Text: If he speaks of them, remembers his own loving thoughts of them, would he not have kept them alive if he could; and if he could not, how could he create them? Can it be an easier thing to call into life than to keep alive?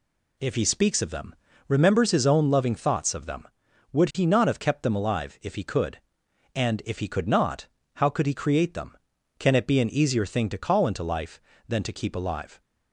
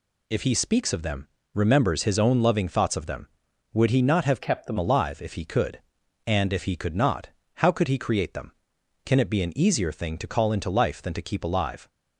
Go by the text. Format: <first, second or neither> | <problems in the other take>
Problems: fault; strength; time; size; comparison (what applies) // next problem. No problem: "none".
first | changes voice from "kept" to "them"; from 4.4 to 4.7 s; 0.3 s long